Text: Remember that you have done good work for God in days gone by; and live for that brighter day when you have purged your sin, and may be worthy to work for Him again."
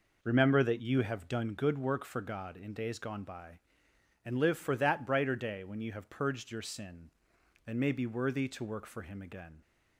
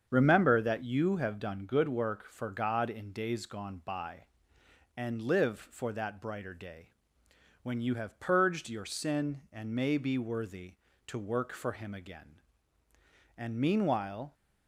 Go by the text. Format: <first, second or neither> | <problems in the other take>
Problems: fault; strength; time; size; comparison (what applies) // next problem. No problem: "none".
first | starts louder than the rest; strong; until 1.1 s; 7.5 dB // pauses between "day" and "when"; noticeable; at 6.9 s; 0.70 s long // goes on to say "And meanwhile"; noticeable; from 13.3 s on; 0.98 s long